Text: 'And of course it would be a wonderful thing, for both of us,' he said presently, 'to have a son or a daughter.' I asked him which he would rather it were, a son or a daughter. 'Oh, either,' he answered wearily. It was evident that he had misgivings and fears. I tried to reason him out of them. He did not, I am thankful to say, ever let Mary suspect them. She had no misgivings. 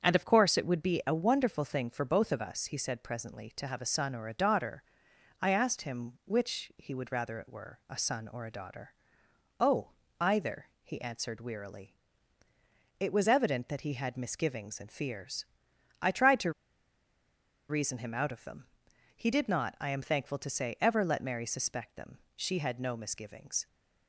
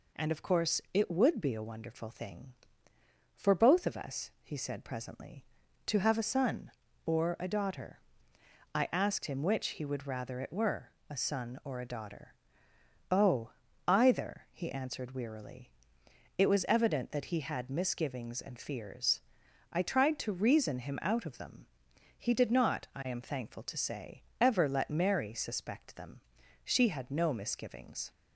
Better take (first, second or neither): second